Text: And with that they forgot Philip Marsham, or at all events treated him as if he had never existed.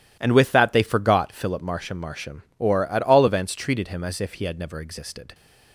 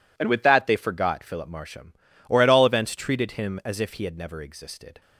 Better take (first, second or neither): second